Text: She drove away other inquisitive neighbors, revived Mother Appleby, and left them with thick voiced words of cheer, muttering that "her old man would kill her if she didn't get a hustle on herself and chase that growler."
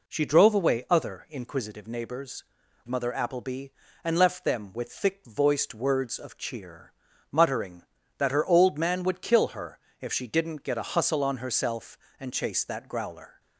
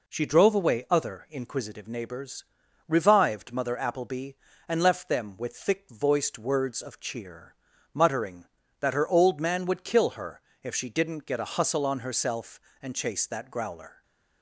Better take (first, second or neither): second